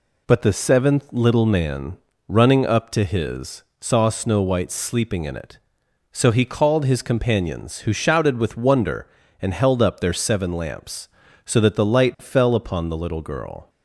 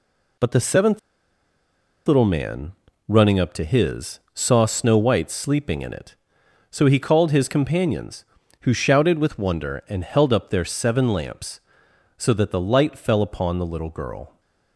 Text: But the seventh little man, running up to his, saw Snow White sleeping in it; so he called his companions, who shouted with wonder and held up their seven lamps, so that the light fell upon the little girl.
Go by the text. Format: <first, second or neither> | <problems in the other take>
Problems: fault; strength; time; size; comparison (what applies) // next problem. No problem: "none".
first | pauses between "seventh" and "little"; at 0.9 s; 1.0 s long